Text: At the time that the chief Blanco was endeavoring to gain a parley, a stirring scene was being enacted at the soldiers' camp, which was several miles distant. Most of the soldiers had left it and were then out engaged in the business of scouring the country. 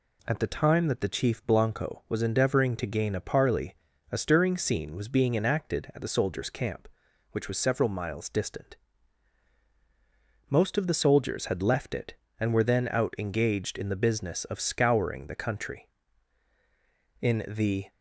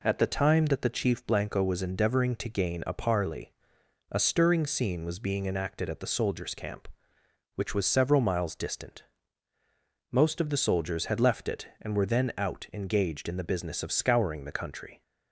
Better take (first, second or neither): second